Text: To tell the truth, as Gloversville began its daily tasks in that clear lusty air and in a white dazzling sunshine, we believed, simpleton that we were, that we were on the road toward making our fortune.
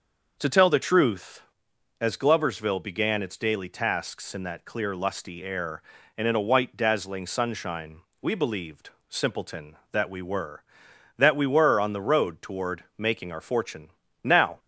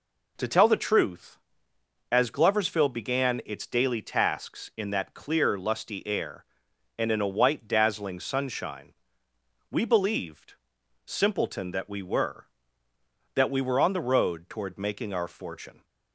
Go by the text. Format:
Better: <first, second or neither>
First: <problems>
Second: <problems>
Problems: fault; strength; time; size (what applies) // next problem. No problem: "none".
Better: second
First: starts louder than the rest; until 1.3 s; 6.5 dB // goes on to say "Now"; slight; from 14.2 s on; 0.36 s long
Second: none